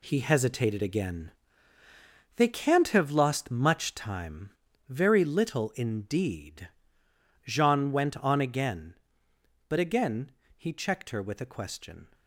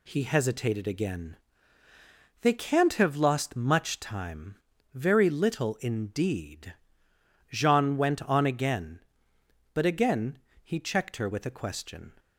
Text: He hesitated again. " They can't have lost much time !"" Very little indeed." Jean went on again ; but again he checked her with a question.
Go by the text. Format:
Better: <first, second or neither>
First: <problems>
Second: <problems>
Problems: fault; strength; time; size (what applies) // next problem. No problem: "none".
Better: second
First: gets quieter; noticeable; throughout; 4 dB // pauses between "again" and "he"; slight; at 10.2 s; 0.26 s long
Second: pauses between "again" and "he"; slight; at 10.3 s; 0.26 s long